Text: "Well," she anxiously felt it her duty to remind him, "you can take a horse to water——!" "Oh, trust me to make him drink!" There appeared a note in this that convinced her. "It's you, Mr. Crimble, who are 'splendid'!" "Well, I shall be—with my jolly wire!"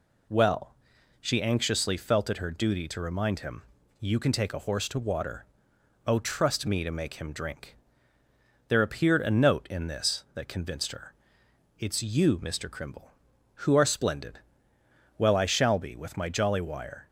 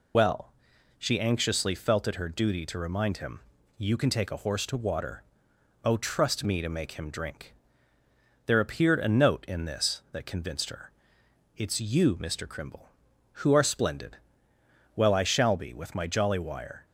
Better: first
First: none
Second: loses the start of "Well"; at 0.1 s; 75 ms

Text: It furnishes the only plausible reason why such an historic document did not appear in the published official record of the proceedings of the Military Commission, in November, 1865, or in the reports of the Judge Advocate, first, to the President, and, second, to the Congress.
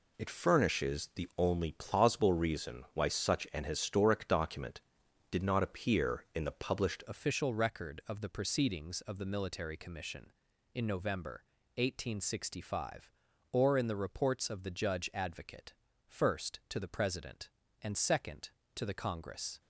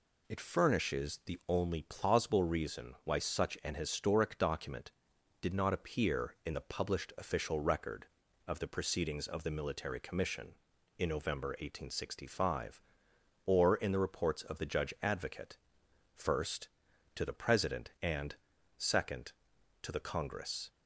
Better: second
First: changes voice at "official"; from 7.0 s on; 12.6 s long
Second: none

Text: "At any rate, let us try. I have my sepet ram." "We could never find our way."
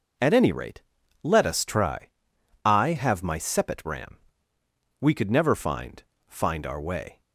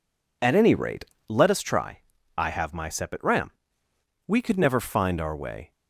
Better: second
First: says "find" twice; at 6.2 s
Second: none

